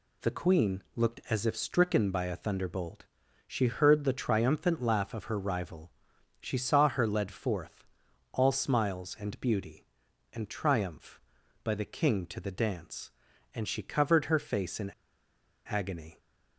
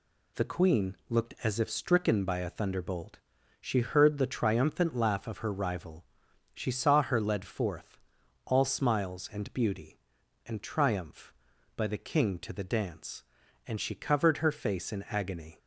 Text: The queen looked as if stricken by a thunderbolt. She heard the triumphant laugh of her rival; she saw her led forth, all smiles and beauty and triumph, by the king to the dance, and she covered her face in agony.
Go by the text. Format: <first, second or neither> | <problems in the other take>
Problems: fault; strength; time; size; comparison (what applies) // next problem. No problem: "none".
second | pauses between "in" and "agony"; noticeable; at 14.9 s; 0.79 s long